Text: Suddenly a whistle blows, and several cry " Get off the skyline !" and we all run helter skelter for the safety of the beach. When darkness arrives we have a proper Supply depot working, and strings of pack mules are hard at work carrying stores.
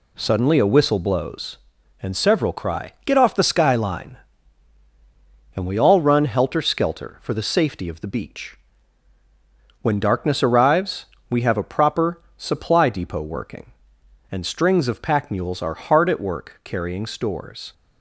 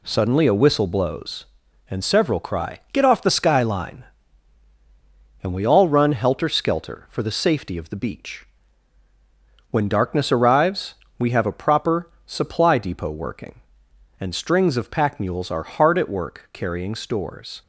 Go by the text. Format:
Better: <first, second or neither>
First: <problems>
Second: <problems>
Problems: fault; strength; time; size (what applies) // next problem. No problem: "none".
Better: neither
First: pauses between "arrives" and "we"; slight; at 11.0 s; 0.24 s long // pauses between "proper" and "Supply"; slight; at 12.2 s; 0.16 s long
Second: pauses between "arrives" and "we"; slight; at 10.9 s; 0.24 s long // pauses between "proper" and "Supply"; slight; at 12.0 s; 0.16 s long